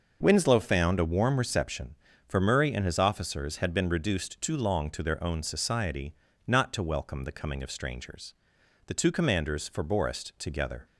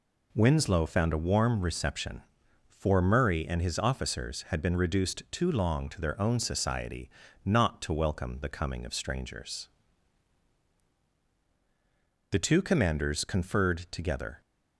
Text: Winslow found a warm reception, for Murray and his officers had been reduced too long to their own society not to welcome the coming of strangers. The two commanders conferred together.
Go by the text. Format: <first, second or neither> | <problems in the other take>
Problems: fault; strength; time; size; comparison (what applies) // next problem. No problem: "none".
second | starts louder than the rest; noticeable; until 1.2 s; 6 dB // pauses between "society" and "not"; slight; at 6.1 s; 0.32 s long; slight in the second // says "forborest" for "conferred"; at 9.6 s